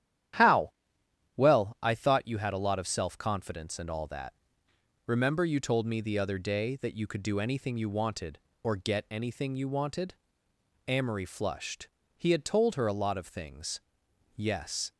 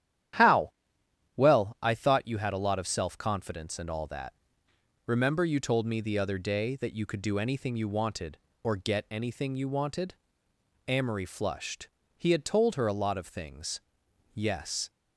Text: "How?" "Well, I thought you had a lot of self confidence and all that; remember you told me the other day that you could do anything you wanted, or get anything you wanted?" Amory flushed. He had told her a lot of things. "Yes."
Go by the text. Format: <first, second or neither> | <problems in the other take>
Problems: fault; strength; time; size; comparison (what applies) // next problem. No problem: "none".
neither | starts louder than the rest; strong; the same in both